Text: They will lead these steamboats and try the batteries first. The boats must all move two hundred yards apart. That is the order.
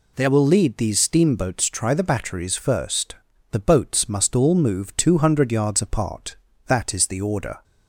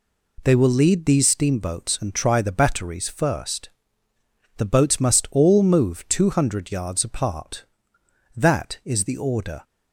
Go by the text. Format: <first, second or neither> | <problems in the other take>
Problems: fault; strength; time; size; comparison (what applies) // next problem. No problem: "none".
second | skips "and"; at 1.6 s